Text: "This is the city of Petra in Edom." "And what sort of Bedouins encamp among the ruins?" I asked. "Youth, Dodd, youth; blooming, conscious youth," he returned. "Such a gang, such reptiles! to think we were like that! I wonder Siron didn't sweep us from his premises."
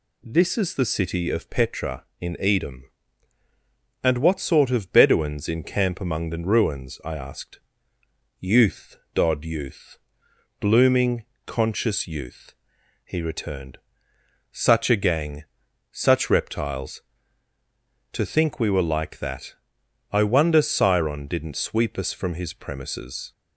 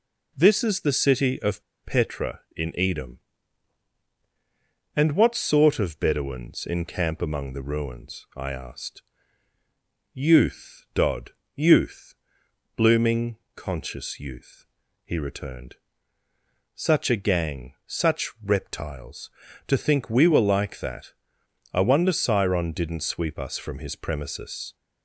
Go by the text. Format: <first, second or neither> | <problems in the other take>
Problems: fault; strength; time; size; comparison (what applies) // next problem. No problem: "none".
first | pauses between "of" and "Petra"; slight; at 1.6 s; 0.20 s long